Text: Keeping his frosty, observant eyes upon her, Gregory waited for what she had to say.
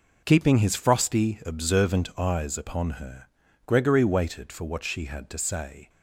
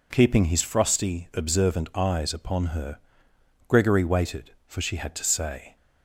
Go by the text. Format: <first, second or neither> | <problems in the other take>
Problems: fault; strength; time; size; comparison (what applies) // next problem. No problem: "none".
first | skips "what"; at 4.8 s